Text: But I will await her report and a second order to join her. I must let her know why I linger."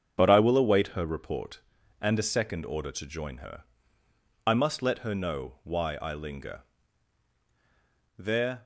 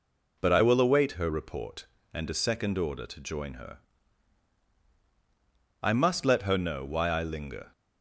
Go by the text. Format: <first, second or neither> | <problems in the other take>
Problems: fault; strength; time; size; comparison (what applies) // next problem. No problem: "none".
second | starts louder than the rest; strong; until 1.1 s; 7 dB // goes on to say "There"; slight; from 8.1 s on; 0.46 s long